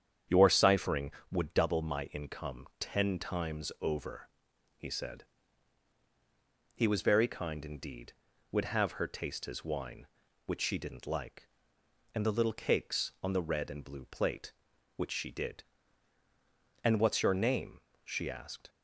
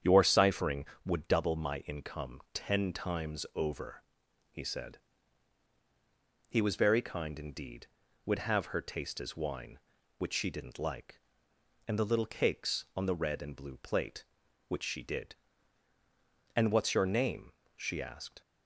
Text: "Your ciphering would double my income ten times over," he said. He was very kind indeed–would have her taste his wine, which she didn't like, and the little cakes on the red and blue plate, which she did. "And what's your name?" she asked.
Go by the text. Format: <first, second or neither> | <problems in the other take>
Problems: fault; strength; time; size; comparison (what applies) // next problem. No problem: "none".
neither | starts louder than the rest; strong; the same in both